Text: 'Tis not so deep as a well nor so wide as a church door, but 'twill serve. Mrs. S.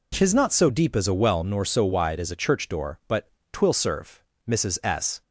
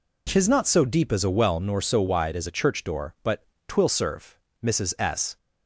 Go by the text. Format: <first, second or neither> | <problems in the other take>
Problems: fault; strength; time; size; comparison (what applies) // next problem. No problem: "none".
neither | pauses between "but" and "twill"; slight; the same in both